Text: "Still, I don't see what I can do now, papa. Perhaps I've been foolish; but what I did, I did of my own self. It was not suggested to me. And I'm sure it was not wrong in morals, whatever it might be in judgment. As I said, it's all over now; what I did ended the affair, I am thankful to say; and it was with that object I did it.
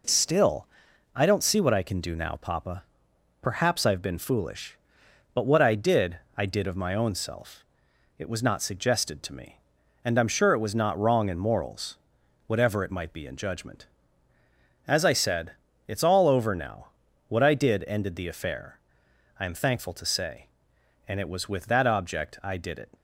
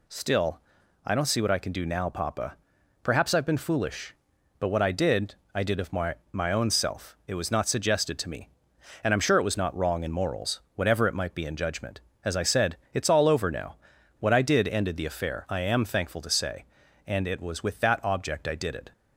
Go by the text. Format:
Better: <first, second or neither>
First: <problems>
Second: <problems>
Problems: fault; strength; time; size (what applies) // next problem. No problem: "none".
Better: first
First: none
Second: says "my" twice; at 6.3 s